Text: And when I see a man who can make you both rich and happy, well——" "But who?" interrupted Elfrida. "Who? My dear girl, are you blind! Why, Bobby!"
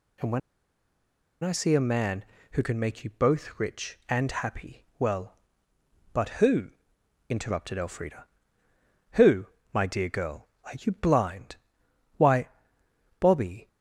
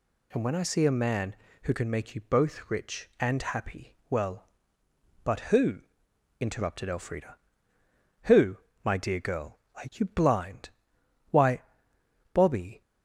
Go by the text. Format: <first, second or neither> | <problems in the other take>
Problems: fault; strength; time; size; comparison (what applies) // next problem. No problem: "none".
second | pauses between "when" and "I"; at 0.3 s; 1.0 s long